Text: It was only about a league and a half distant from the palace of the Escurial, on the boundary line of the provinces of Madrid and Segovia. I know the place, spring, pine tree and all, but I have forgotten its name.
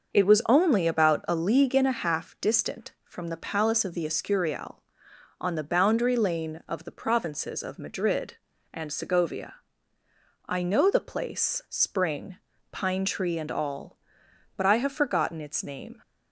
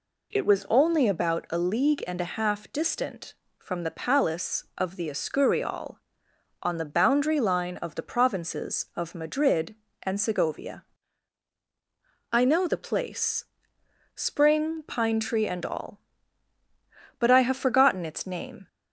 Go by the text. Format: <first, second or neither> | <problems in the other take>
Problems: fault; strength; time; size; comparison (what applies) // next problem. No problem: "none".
second | starts louder than the rest; until 1.1 s; 6 dB // says "lane" for "line"; at 6.1 s